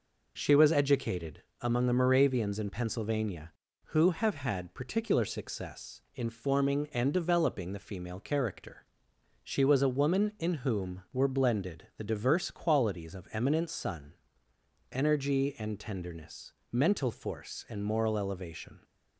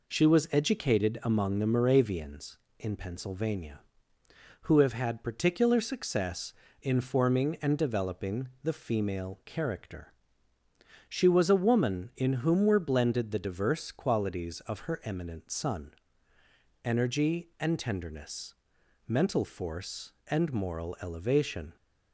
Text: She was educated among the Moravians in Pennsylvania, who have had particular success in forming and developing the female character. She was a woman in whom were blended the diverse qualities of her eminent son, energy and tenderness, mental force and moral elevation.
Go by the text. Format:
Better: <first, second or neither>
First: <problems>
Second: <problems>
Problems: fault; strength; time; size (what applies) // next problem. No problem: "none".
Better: second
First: pauses between "educated" and "among"; slight; at 1.4 s; 0.22 s long // skips "her"; at 13.2 s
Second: none